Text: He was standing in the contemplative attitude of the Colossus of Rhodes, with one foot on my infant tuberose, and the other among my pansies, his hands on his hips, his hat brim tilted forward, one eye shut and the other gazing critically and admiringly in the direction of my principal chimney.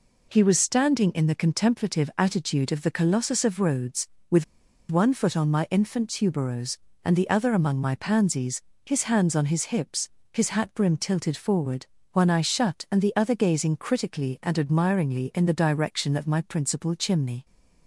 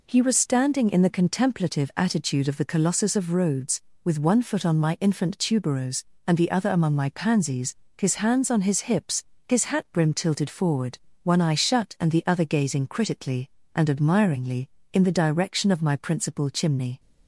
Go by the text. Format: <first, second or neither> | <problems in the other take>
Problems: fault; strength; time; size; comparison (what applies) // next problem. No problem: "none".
second | pauses between "with" and "one"; at 4.4 s; 0.44 s long